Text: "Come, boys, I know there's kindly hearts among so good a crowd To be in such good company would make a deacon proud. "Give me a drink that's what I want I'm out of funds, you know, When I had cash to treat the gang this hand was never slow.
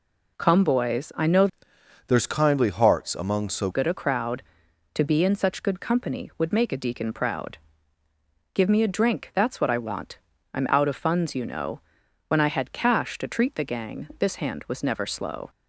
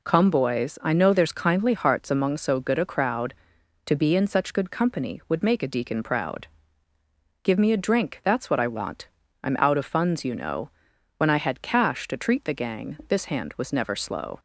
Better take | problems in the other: second | changes voice from "there's" to "so"; from 2.0 to 3.6 s; 1.6 s long // pauses between "want" and "I'm"; slight; at 10.1 s; 0.34 s long; slight in the second

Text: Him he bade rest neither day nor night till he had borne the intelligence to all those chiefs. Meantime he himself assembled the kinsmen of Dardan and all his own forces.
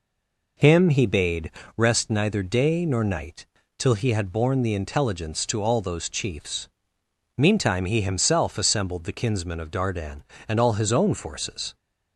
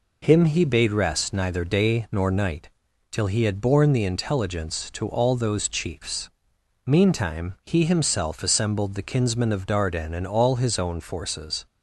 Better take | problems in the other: second | stays silent before the first word; slight; until 0.5 s; 0.5 s long // pauses between "bade" and "rest"; slight; at 1.5 s; 0.24 s long // pauses between "night" and "till"; slight; at 3.4 s; 0.32 s long; also in the second

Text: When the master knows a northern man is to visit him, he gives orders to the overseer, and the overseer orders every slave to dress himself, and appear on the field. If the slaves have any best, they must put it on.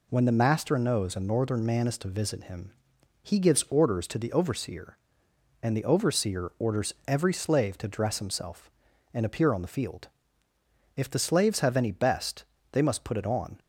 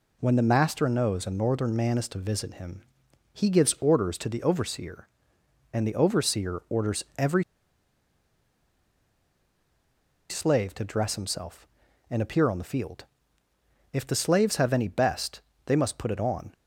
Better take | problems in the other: first | pauses between "every" and "slave"; strong; at 7.4 s; 2.8 s long

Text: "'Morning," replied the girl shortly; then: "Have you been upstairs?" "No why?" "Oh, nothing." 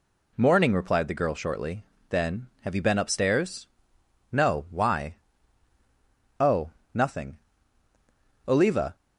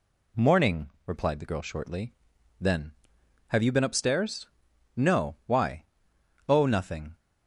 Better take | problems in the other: second | goes on to say "Oliva"; slight; from 8.4 s on; 0.48 s long

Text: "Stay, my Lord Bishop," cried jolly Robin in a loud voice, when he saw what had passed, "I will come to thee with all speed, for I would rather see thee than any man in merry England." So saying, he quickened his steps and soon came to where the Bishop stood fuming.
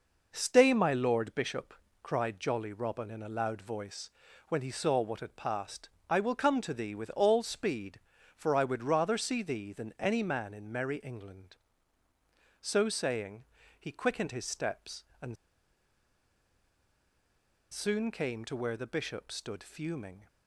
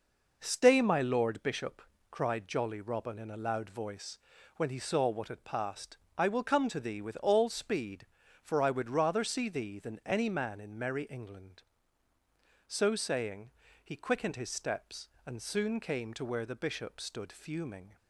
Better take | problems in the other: second | pauses between "and" and "soon"; strong; at 15.3 s; 2.3 s long

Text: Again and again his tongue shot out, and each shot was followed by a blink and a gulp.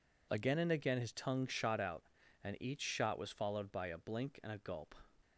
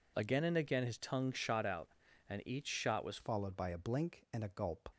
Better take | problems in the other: first | changes voice at "followed"; from 3.1 s on; 1.7 s long

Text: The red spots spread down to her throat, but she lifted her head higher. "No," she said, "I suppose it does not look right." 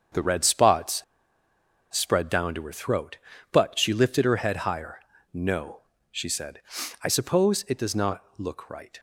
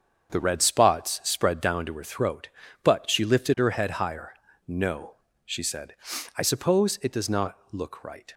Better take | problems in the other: second | starts louder than the rest; strong; until 2.0 s; 7 dB; strong in the second // pauses between "spots" and "spread"; noticeable; at 1.0 s; 0.92 s long // pauses between "not" and "look"; slight; at 8.2 s; 0.16 s long; slight in the second

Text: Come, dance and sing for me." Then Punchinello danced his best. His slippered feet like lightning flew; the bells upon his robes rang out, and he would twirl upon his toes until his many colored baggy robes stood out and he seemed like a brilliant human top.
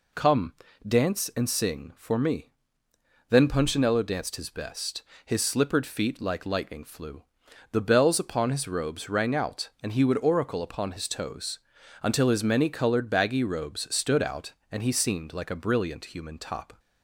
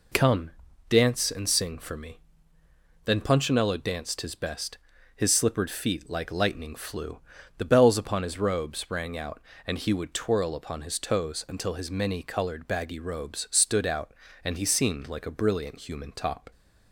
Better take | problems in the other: second | says "oracle" for "twirl"; at 10.1 s // pauses between "toes" and "until"; at 11.5 s; 0.42 s long

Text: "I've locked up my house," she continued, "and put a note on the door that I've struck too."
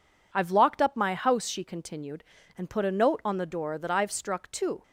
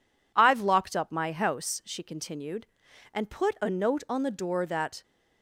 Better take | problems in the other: first | stops before "I've struck too"; at 5.0 s

